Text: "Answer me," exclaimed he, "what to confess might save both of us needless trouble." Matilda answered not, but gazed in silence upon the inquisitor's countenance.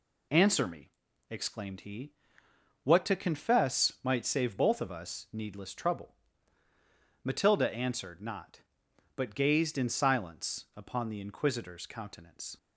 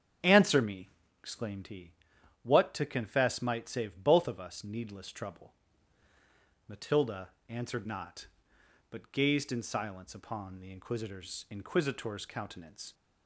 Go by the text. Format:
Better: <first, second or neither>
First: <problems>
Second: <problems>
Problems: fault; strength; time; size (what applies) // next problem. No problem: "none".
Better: first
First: none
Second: starts louder than the rest; strong; until 1.5 s; 7.5 dB // pauses between "Matilda" and "answered"; slight; at 7.2 s; 0.18 s long // says "inquisitor's" twice; at 11.5 s